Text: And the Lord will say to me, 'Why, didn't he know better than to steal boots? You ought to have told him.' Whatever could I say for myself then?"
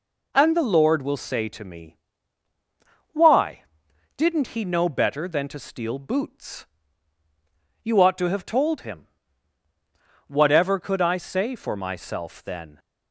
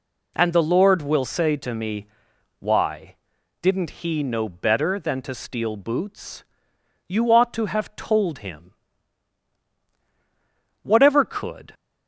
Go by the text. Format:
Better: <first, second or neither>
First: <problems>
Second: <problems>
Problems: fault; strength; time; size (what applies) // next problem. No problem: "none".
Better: first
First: none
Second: stops before "I say for myself then"; at 11.7 s